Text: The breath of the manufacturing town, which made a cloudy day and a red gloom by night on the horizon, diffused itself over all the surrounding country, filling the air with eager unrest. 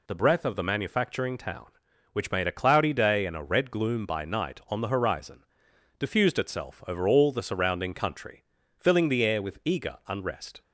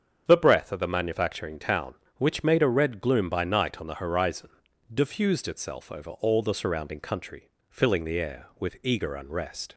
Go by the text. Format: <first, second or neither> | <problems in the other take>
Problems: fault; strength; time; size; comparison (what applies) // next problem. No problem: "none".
first | starts louder than the rest; strong; until 1.2 s; 7.5 dB // skips "cloudy day and a"; at 2.6 s